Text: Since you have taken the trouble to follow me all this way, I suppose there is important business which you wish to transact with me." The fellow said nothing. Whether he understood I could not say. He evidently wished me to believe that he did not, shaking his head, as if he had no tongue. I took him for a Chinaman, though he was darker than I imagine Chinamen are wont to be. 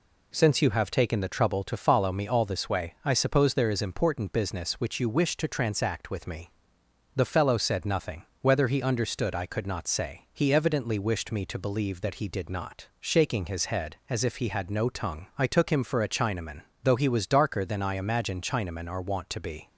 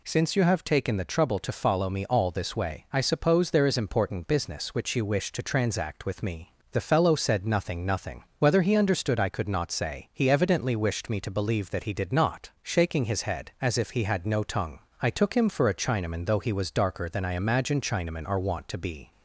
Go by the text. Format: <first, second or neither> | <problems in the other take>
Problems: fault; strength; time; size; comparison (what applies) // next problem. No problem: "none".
first | says "nothing" twice; at 7.8 s